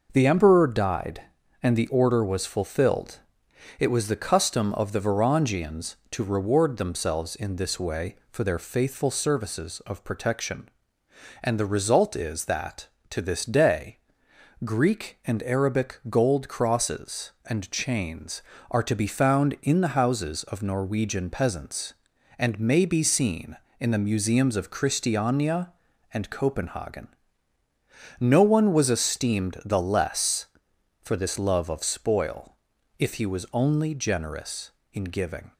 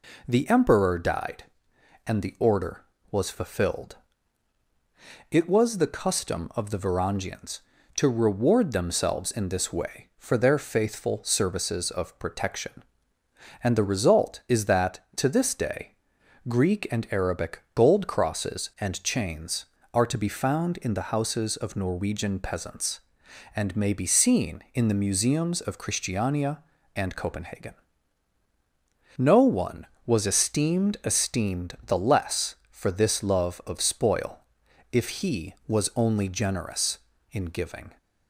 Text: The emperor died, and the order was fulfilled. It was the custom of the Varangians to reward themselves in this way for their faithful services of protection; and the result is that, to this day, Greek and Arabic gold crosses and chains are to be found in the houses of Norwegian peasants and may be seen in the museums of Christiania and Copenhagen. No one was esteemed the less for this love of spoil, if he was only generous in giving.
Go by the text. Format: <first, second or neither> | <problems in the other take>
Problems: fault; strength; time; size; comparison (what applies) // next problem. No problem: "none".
first | says "esteemed" twice; at 31.0 s